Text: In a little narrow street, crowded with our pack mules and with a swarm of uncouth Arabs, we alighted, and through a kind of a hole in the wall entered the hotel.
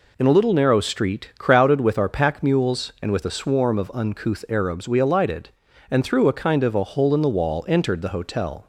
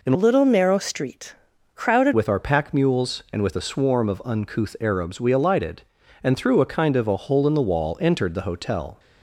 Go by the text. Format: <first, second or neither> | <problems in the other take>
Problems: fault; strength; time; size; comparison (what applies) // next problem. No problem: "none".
first | changes voice from "little" to "crowded"; from 0.1 to 2.1 s; 2.0 s long